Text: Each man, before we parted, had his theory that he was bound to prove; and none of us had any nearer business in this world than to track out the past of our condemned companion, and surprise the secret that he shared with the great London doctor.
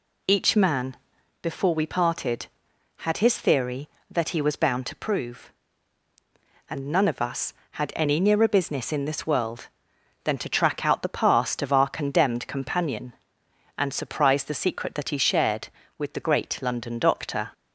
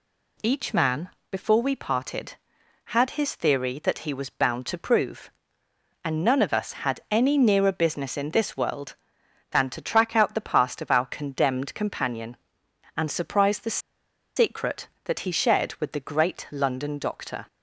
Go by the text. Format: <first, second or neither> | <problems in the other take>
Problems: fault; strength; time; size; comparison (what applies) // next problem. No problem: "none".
first | pauses between "the" and "secret"; noticeable; at 13.7 s; 0.58 s long